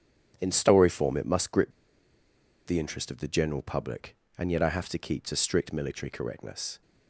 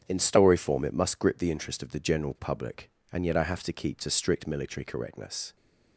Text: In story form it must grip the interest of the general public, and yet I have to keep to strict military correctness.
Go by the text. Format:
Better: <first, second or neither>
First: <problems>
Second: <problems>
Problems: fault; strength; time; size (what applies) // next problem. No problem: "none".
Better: second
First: starts louder than the rest; strong; until 1.4 s; 8 dB // pauses between "grip" and "the"; noticeable; at 1.7 s; 0.96 s long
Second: starts louder than the rest; strong; until 1.0 s; 8 dB